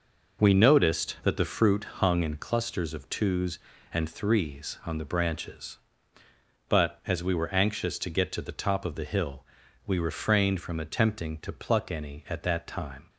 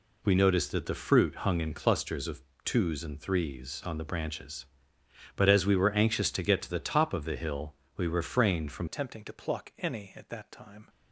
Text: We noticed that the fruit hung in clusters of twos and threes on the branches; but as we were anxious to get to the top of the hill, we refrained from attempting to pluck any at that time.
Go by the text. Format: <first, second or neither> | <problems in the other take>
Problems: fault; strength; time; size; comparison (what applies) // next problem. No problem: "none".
first | pauses between "of" and "twos"; slight; at 2.4 s; 0.20 s long // changes voice at "attempting"; from 8.8 s on; 2.0 s long